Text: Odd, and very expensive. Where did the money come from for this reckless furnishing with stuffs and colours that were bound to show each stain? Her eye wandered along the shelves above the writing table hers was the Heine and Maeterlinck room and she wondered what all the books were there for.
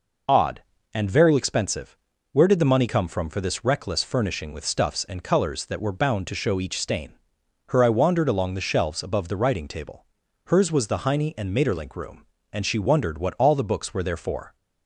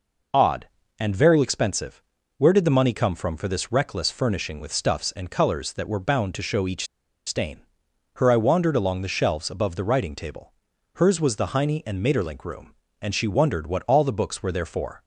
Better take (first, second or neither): first